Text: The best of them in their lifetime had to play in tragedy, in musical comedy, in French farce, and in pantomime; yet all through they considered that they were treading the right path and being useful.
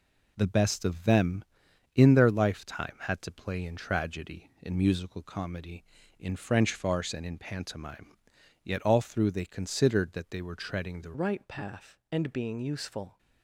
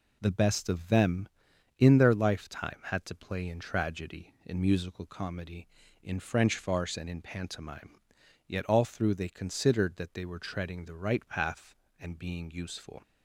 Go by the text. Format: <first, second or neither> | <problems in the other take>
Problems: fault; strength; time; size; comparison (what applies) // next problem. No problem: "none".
second | changes voice at "right"; from 11.1 s on; 2.0 s long